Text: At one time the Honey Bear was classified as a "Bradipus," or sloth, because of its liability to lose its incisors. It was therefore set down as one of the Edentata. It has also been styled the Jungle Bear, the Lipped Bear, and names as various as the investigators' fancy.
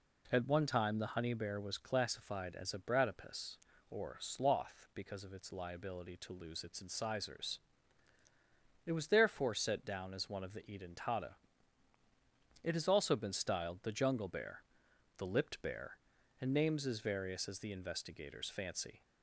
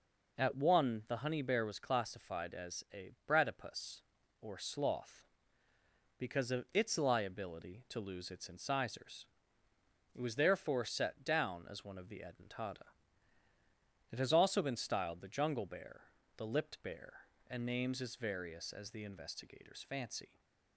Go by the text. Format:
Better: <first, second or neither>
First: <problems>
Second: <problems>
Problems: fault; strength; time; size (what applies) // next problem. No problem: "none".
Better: first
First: none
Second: skips "time"; at 1.0 s // pauses between "a" and "Bradipus"; slight; at 3.1 s; 0.16 s long